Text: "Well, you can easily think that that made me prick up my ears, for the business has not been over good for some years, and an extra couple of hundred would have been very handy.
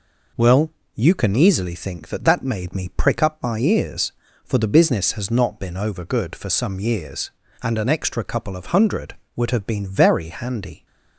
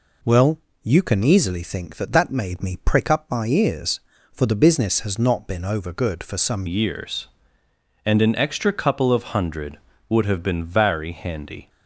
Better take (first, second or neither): first